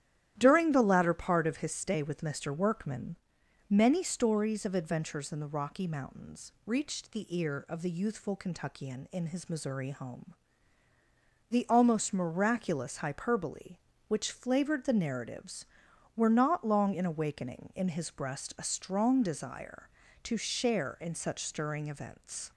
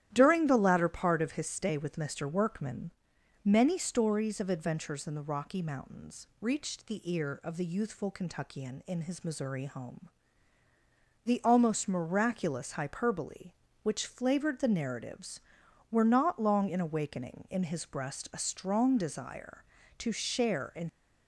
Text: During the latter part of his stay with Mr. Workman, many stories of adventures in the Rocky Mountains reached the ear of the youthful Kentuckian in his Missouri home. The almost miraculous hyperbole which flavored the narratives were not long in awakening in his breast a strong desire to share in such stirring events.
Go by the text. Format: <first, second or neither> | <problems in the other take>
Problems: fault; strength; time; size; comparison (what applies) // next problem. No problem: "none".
first | starts louder than the rest; strong; until 1.1 s; 12 dB; strong in the first // stops before "such stirring events"; at 20.8 s